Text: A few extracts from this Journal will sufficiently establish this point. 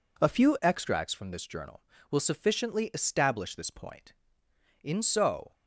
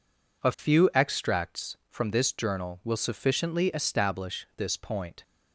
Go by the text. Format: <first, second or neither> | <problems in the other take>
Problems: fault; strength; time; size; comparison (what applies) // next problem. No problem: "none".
second | goes on to say "In so"; noticeable; from 4.8 s on; 0.70 s long